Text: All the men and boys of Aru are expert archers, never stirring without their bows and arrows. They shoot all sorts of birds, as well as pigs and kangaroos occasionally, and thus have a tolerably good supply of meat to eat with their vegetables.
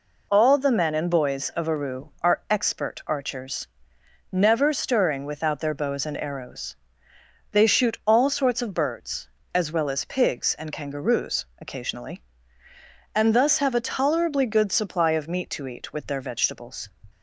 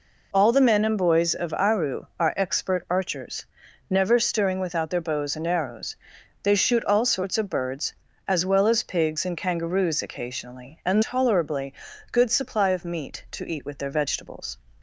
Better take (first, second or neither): first